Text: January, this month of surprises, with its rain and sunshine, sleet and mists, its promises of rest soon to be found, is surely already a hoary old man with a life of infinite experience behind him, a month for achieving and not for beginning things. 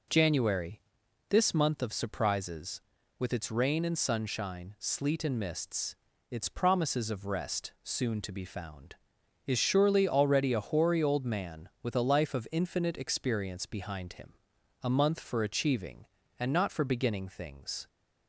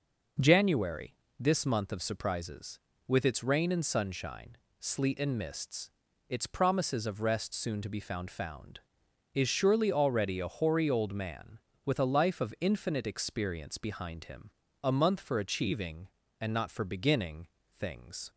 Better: first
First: none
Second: says "found" twice; at 8.2 s // pauses between "beginning" and "things"; slight; at 17.4 s; 0.32 s long

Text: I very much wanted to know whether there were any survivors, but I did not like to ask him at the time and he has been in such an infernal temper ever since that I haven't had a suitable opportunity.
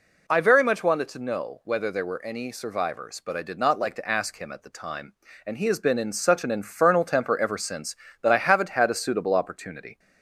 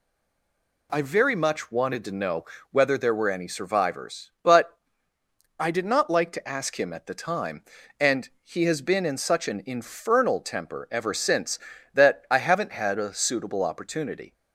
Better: first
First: none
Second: stays silent before the first word; slight; until 0.9 s; 0.9 s long // pauses between "know" and "whether"; slight; at 2.4 s; 0.26 s long // pauses between "but" and "I"; noticeable; at 4.7 s; 0.82 s long

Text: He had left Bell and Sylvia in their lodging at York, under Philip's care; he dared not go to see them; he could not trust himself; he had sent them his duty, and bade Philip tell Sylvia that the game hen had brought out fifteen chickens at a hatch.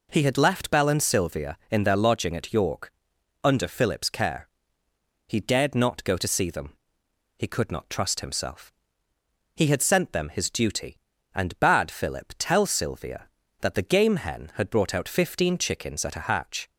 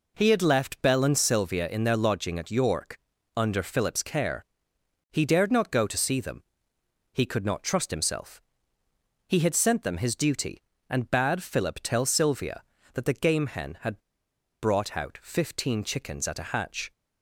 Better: first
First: none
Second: pauses between "had" and "brought"; noticeable; at 13.9 s; 0.63 s long

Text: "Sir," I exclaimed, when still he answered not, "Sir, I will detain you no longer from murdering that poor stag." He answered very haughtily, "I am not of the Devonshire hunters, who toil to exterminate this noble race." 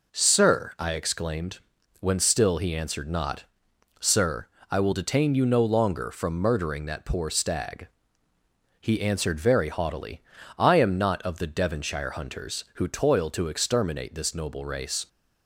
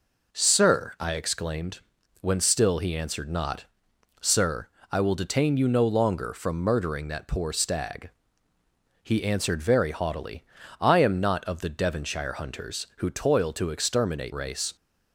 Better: first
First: none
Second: skips "this noble"; at 14.3 s

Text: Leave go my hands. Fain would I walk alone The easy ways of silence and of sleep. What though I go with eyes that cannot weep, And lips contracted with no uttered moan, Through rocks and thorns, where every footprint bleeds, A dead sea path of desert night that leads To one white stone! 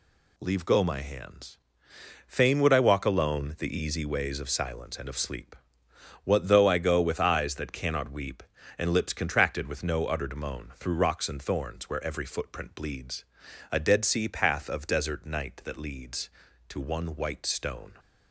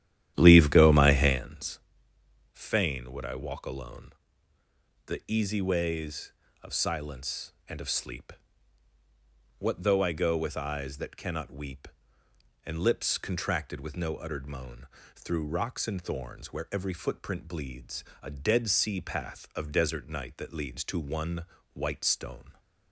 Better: first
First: none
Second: starts louder than the rest; strong; until 1.5 s; 11.5 dB // pauses between "alone" and "The"; noticeable; at 4.1 s; 0.96 s long // pauses between "one" and "white"; slight; at 21.4 s; 0.30 s long

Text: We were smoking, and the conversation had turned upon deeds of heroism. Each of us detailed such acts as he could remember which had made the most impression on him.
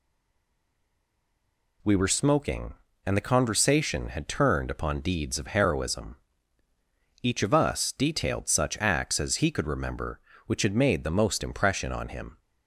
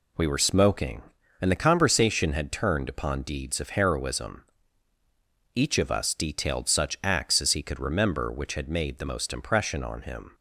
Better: second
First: stays silent before the first word; noticeable; until 1.8 s; 1.8 s long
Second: none

